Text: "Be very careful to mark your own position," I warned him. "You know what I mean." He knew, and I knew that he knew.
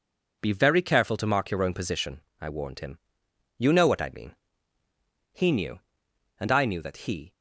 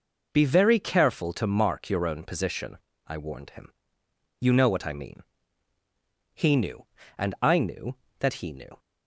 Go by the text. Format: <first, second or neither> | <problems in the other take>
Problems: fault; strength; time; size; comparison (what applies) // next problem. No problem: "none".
second | stops before "knew"; at 7.3 s